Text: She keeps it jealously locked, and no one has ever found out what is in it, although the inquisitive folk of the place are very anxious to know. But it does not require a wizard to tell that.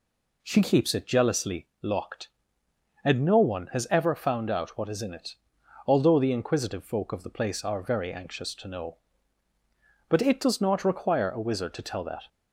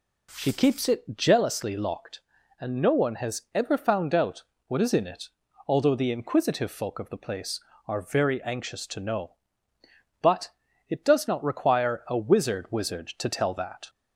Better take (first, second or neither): first